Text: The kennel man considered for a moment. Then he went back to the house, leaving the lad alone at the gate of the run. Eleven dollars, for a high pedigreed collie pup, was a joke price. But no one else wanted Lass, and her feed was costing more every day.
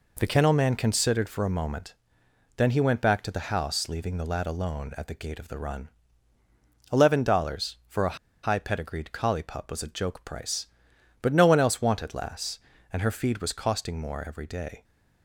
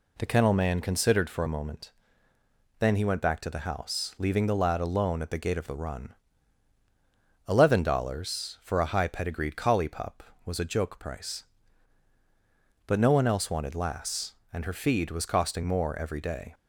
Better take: second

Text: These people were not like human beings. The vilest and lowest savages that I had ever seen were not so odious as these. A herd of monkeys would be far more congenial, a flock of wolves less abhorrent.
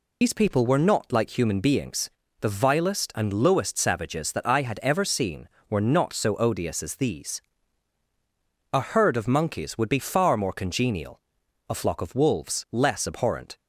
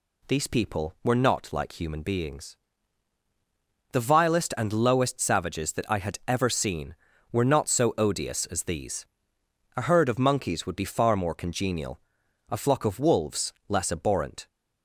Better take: second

